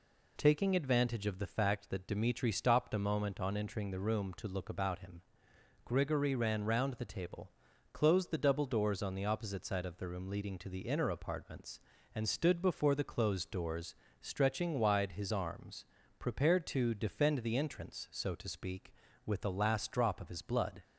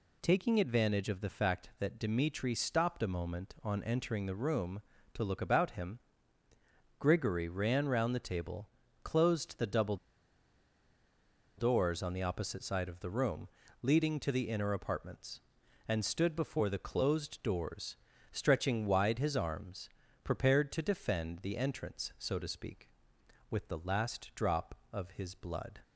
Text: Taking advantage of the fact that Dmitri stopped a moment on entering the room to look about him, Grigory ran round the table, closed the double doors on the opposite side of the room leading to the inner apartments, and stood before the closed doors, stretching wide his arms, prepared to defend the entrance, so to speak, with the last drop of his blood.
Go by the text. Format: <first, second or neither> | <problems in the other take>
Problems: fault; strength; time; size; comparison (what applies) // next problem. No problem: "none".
first | pauses between "double" and "doors"; strong; at 9.9 s; 1.6 s long // pauses between "room" and "leading"; slight; at 13.4 s; 0.34 s long